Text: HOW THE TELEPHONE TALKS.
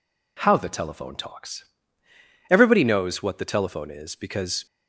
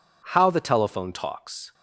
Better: second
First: goes on to say "Everybody knows what the telephone is because"; strong; from 2.4 s on; 2.1 s long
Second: none

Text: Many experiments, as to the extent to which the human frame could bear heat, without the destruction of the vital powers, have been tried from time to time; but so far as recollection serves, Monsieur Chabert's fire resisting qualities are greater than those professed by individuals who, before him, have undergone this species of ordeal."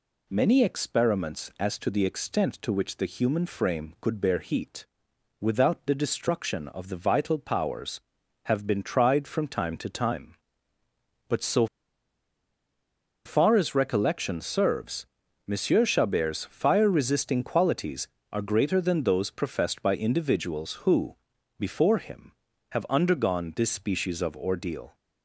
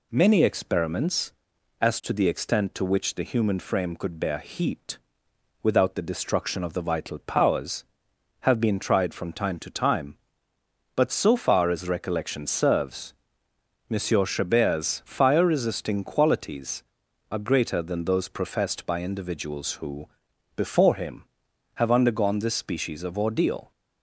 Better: second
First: pauses between "so" and "far"; strong; at 11.6 s; 1.6 s long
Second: none

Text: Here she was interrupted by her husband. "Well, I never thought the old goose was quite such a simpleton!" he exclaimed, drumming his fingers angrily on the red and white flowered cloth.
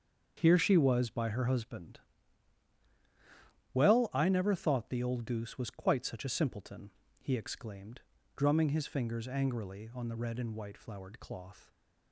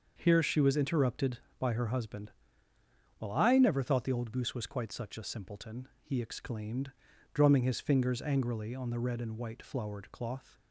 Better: second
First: starts louder than the rest; until 1.4 s; 7 dB // skips "interrupted"; at 1.1 s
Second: starts louder than the rest; until 1.1 s; 6 dB

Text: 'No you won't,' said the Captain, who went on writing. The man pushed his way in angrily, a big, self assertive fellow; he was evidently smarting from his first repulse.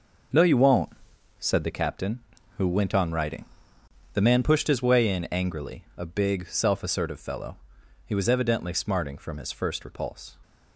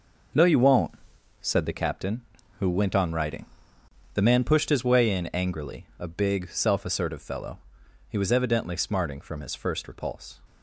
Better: neither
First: none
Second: none

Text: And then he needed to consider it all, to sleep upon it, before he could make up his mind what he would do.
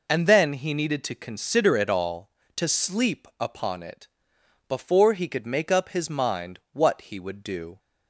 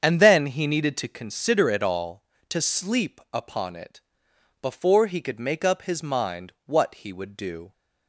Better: first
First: none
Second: starts louder than the rest; strong; until 1.2 s; 7.5 dB

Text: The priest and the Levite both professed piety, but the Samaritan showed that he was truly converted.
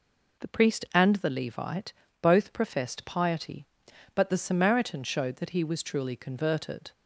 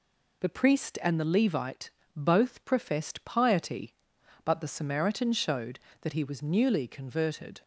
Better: first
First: pauses between "Levite" and "both"; slight; at 1.9 s; 0.26 s long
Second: pauses between "Levite" and "both"; slight; at 1.8 s; 0.26 s long // says "newly" for "truly"; at 6.4 s

